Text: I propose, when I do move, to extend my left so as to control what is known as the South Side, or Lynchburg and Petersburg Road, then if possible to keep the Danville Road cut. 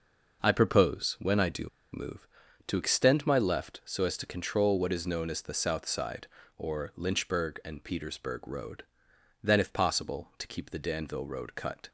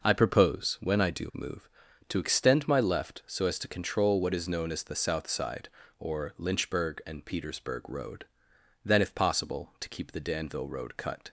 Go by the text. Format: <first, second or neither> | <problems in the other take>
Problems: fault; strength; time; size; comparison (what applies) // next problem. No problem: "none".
second | pauses between "do" and "move"; slight; at 1.6 s; 0.25 s long